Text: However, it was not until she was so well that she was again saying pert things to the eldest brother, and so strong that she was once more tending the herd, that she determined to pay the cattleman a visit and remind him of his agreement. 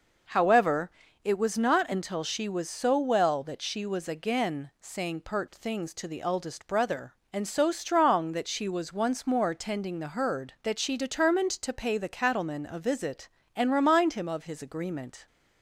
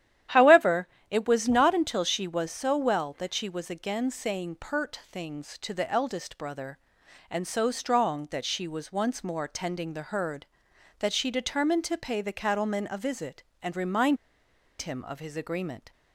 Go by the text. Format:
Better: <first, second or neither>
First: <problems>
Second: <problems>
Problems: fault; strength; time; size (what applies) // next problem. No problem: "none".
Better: first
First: none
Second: starts louder than the rest; strong; until 1.5 s; 11 dB // pauses between "remind" and "him"; noticeable; at 14.1 s; 0.64 s long